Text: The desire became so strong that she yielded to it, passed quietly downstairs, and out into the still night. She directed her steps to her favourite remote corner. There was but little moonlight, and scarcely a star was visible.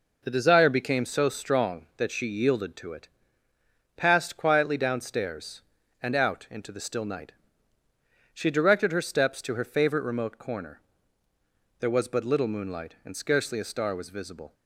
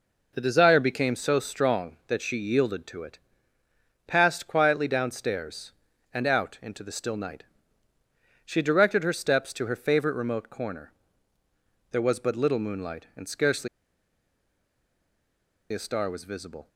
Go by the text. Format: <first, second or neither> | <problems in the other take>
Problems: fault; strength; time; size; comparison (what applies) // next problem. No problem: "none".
first | pauses between "scarcely" and "a"; strong; at 13.6 s; 2.0 s long